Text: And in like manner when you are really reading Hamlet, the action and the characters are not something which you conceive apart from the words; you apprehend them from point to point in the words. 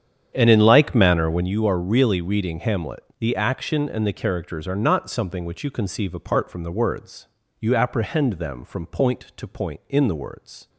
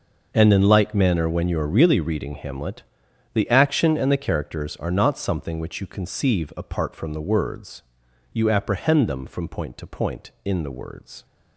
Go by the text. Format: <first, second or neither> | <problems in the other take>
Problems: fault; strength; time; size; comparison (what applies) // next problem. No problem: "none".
second | starts louder than the rest; strong; until 1.5 s; 8.5 dB